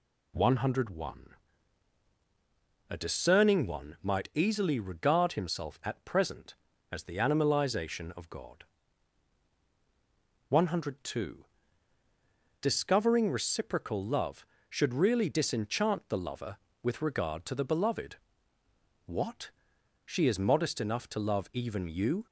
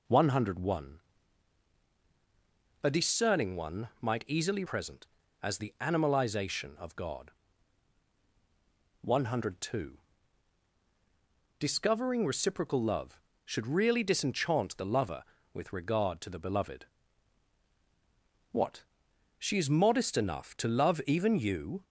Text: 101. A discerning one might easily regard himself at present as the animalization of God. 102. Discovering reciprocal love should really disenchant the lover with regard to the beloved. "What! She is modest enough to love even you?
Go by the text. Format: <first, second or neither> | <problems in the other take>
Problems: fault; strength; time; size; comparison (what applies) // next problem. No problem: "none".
first | skips "regard himself at"; at 4.6 s